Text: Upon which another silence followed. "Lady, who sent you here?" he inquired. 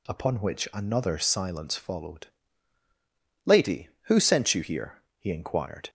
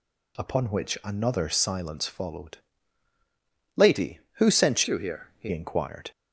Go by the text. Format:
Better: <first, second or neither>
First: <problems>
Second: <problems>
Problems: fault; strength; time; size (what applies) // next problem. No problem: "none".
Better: first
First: none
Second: changes voice from "you" to "he"; from 4.8 to 5.4 s; 0.6 s long